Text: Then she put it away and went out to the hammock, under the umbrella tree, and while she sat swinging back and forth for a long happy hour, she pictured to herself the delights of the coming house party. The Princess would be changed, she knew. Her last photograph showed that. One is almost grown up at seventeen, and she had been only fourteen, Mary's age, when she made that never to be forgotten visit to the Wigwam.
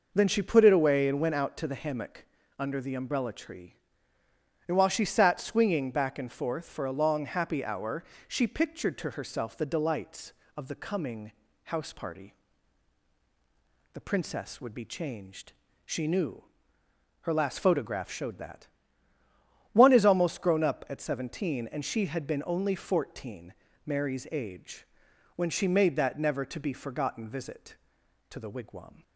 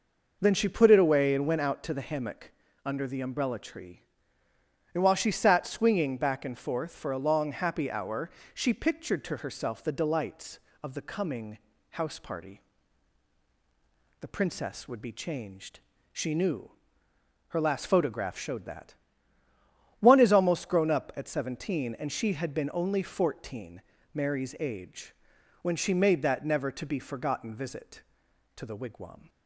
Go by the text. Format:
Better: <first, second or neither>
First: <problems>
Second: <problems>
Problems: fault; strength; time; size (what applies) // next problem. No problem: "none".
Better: neither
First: pauses between "coming" and "house"; slight; at 11.3 s; 0.32 s long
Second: pauses between "coming" and "house"; slight; at 11.5 s; 0.32 s long